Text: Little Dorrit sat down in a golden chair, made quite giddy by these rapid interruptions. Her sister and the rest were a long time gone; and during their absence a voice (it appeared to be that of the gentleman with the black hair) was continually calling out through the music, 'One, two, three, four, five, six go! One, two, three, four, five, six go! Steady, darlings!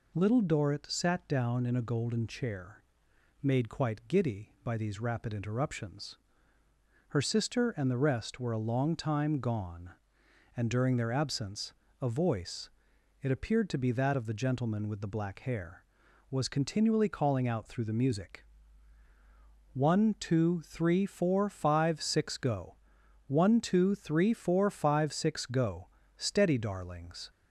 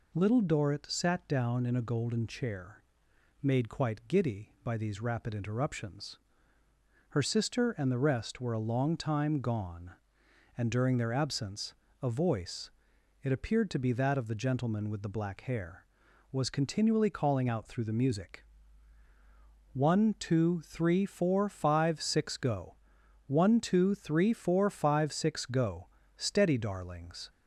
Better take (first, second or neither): neither